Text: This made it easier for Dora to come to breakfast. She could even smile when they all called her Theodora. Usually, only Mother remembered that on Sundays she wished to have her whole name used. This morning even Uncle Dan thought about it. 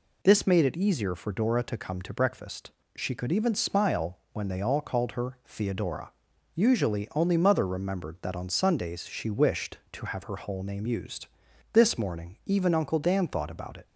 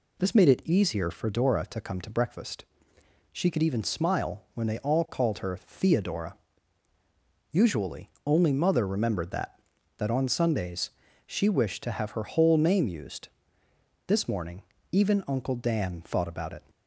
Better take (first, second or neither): first